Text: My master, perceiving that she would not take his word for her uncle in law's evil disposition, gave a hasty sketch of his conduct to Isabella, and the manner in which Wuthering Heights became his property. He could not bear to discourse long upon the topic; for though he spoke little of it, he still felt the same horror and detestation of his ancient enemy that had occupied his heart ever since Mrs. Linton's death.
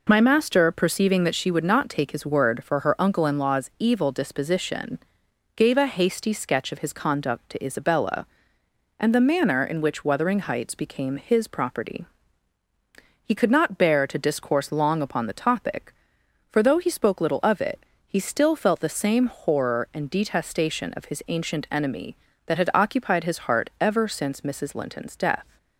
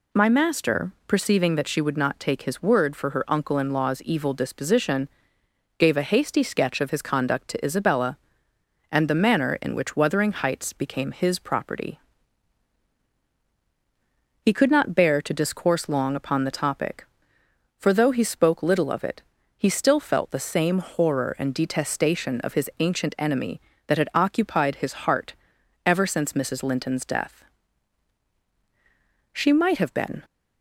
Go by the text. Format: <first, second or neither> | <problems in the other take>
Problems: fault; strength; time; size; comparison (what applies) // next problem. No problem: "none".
first | pauses between "heart" and "ever"; noticeable; at 25.3 s; 0.50 s long // goes on to say "She might have been"; noticeable; from 29.3 s on; 0.90 s long